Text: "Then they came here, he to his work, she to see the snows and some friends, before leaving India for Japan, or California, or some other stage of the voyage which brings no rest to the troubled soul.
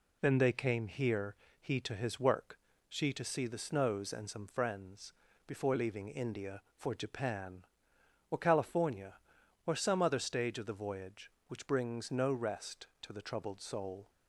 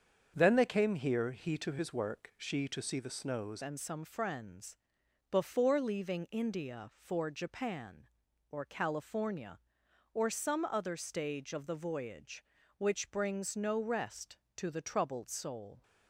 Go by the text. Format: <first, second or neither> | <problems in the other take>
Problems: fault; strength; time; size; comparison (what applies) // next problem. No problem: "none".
first | starts louder than the rest; strong; until 1.3 s; 7 dB // changes voice at "and"; from 3.6 s on; 12.2 s long